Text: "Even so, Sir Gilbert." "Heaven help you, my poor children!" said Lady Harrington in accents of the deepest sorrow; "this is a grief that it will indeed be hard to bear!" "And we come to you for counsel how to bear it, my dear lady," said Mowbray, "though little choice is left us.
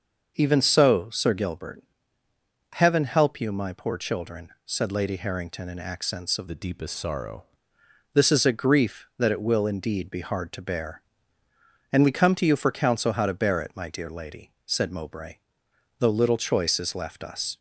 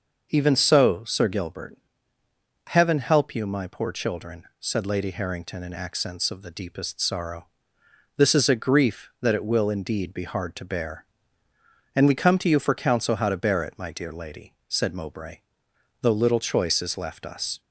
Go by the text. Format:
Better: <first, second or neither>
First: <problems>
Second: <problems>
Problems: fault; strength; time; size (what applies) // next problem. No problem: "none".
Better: second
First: starts louder than the rest; noticeable; until 1.3 s; 6 dB // changes voice from "the" to "sorrow"; from 6.4 to 7.4 s; 1.0 s long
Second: none